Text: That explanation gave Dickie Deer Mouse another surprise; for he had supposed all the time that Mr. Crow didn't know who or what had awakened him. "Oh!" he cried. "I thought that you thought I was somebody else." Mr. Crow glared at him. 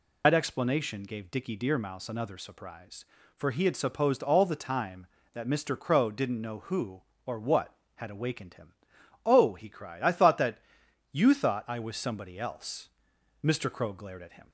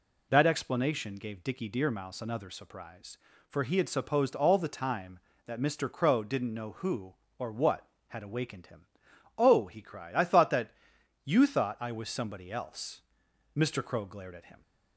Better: second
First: loses the start of "That"; at 0.2 s; 80 ms // pauses between "that" and "you"; noticeable; at 10.5 s; 0.54 s long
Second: pauses between "that" and "you"; noticeable; at 10.7 s; 0.54 s long

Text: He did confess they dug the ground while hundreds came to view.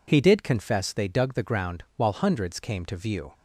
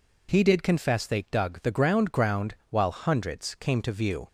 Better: first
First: none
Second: says "ground" twice; at 2.1 s

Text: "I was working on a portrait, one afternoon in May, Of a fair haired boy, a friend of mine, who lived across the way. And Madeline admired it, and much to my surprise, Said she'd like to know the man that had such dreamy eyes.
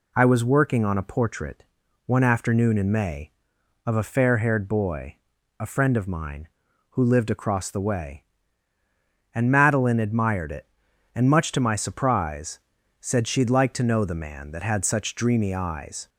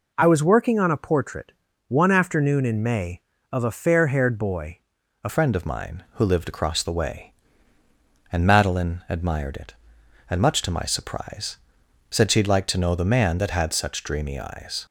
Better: first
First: none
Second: changes voice at "friend"; from 5.2 s on; 9.6 s long

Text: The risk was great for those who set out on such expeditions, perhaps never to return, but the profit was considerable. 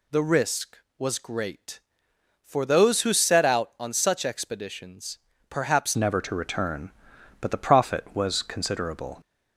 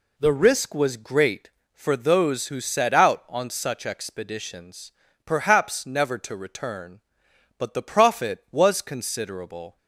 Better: second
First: changes voice at "never"; from 5.9 s on; 3.3 s long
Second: none

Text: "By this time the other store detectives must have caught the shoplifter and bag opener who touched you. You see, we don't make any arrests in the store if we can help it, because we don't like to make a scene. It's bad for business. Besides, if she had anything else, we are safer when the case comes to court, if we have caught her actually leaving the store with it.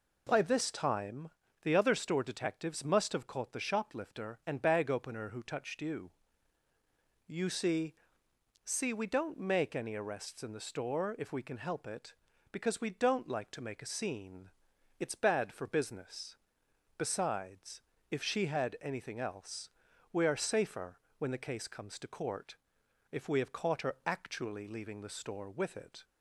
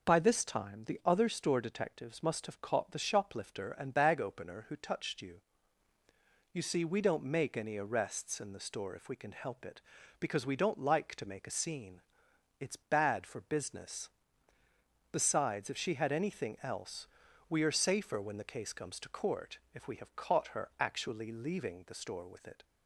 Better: second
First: pauses between "time" and "the"; slight; at 1.2 s; 0.32 s long // says "see" twice; at 8.6 s // pauses between "safer" and "when"; slight; at 20.9 s; 0.20 s long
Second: none

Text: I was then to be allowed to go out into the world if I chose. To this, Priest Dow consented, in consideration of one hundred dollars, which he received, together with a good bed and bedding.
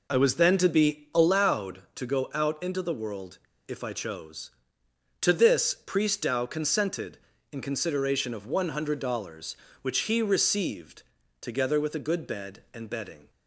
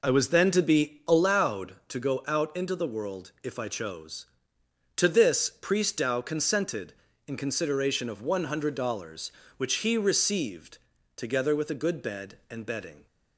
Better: second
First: pauses between "world" and "if"; slight; at 3.3 s; 0.30 s long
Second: none

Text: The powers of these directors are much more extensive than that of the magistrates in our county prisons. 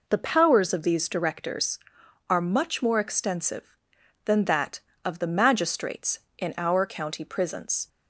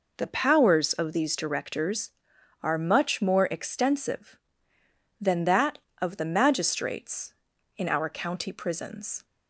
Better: neither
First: none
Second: none

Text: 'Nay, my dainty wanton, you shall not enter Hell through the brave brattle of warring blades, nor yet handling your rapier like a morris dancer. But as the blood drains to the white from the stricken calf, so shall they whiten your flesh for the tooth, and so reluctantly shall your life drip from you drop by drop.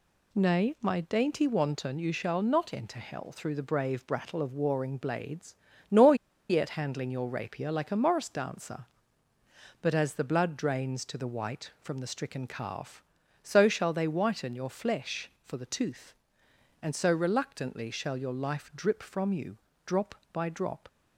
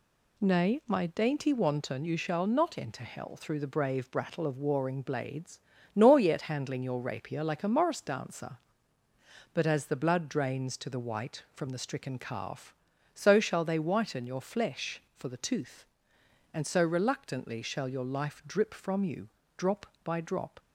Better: second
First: pauses between "nor" and "yet"; slight; at 6.1 s; 0.34 s long // pauses between "you" and "drop"; slight; at 19.5 s; 0.28 s long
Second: pauses between "you" and "drop"; slight; at 19.2 s; 0.28 s long

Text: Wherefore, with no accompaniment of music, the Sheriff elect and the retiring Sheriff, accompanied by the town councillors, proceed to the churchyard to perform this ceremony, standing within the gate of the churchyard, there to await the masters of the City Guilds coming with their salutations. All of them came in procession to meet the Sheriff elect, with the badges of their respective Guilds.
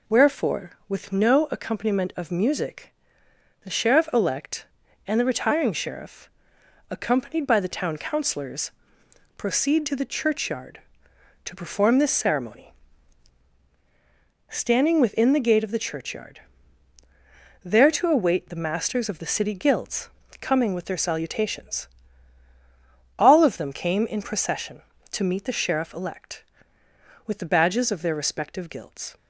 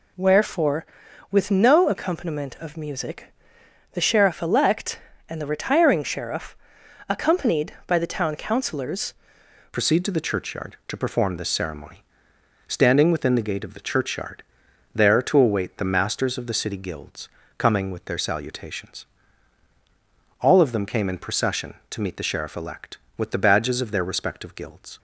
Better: first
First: pauses between "Guilds" and "coming"; slight; at 20.0 s; 0.32 s long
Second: changes voice at "proceed"; from 9.7 s on; 15.2 s long // pauses between "Guilds" and "coming"; slight; at 17.2 s; 0.28 s long

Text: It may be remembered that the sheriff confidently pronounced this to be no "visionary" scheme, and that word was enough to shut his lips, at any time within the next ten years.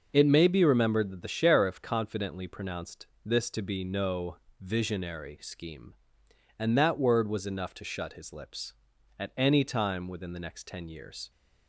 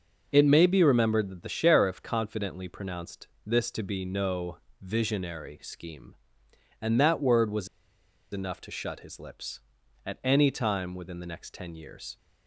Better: first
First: pauses between "pronounced" and "this"; slight; at 3.0 s; 0.20 s long // pauses between "no" and "visionary"; slight; at 4.3 s; 0.20 s long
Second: pauses between "pronounced" and "this"; slight; at 3.2 s; 0.20 s long // pauses between "no" and "visionary"; slight; at 4.5 s; 0.20 s long // pauses between "was" and "enough"; noticeable; at 7.6 s; 0.65 s long

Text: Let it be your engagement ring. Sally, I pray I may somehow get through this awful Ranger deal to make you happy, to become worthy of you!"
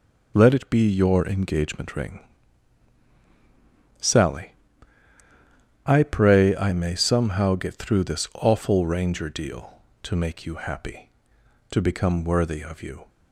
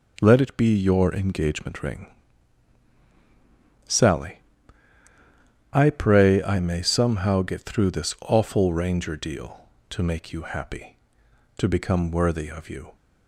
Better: second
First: loses the start of "Let"; at 0.3 s; 30 ms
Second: none

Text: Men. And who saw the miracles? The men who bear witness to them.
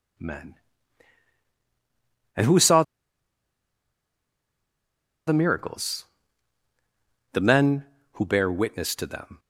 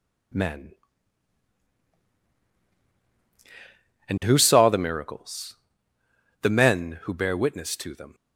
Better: second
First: pauses between "saw" and "the"; strong; at 2.8 s; 2.4 s long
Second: none

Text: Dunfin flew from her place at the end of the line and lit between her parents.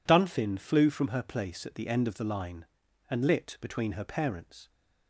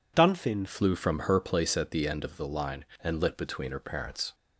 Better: first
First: none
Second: changes voice at "flew"; from 0.6 s on; 3.7 s long

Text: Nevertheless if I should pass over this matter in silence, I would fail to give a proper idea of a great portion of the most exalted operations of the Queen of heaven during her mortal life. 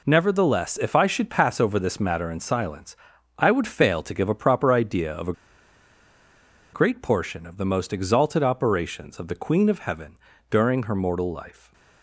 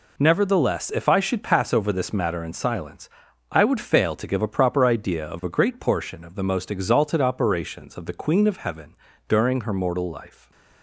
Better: second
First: pauses between "a" and "great"; strong; at 5.3 s; 1.4 s long // pauses between "heaven" and "during"; slight; at 10.1 s; 0.34 s long // stays silent after the last word; slight; from 11.5 s on; 0.5 s long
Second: pauses between "heaven" and "during"; slight; at 8.9 s; 0.34 s long // stays silent after the last word; slight; from 10.2 s on; 0.6 s long

